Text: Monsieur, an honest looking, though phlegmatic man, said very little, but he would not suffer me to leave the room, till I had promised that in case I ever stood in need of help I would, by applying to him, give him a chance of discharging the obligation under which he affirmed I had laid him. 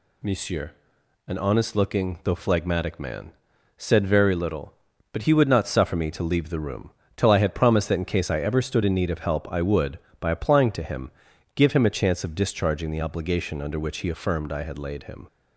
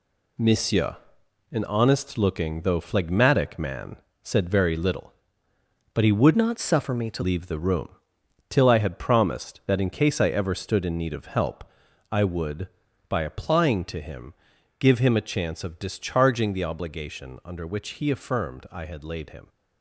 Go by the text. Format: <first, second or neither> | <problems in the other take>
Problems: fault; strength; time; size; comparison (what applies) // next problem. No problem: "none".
first | changes voice from "not" to "to"; from 6.3 to 7.2 s; 0.9 s long // pauses between "help" and "I"; noticeable; at 11.6 s; 0.48 s long